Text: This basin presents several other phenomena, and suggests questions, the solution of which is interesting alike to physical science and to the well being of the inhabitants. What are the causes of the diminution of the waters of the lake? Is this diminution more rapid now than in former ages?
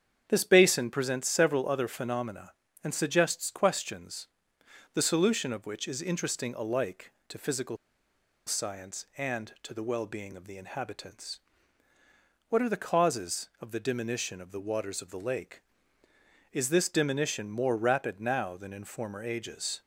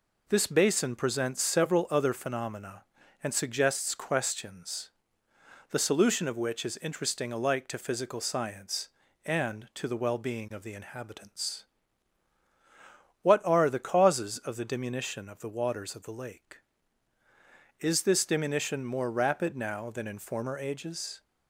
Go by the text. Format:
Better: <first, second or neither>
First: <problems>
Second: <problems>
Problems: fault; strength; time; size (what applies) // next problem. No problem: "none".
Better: second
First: starts louder than the rest; strong; until 1.2 s; 8 dB // pauses between "physical" and "science"; noticeable; at 7.7 s; 0.70 s long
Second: none